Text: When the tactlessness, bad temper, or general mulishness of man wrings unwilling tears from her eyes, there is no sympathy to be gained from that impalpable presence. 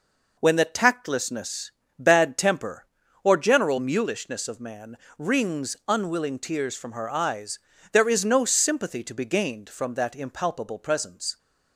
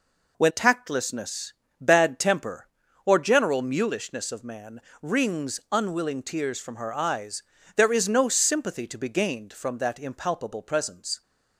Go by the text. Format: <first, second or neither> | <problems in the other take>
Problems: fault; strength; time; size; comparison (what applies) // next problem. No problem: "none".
first | skips "the"; at 0.4 s // pauses between "man" and "wrings"; slight; at 4.8 s; 0.20 s long; slight in the first